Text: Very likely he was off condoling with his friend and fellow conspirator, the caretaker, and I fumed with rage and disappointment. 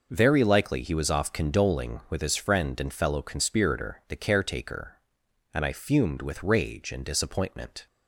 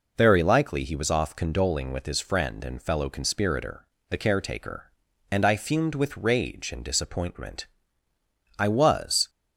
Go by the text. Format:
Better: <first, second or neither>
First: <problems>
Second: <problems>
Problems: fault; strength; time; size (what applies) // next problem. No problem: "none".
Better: first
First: none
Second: goes on to say "I was"; noticeable; from 8.5 s on; 0.70 s long